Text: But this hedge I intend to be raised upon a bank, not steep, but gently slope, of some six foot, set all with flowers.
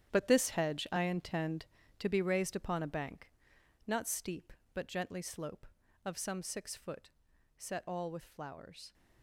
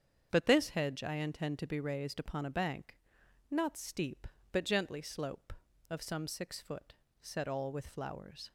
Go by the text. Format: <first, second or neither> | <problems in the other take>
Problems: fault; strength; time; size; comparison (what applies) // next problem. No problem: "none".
second | gets quieter; strong; throughout; 12.5 dB // starts louder than the rest; strong; until 1.1 s; 10 dB; strong in the second